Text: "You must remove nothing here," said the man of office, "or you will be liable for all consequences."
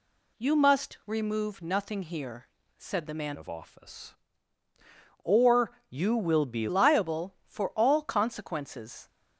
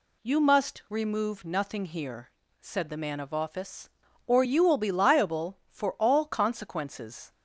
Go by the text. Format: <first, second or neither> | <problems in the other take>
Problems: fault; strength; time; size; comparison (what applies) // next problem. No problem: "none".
second | changes voice from "of" to "be"; from 3.3 to 6.6 s; 3.3 s long // pauses between "or" and "you"; slight; at 5.7 s; 0.20 s long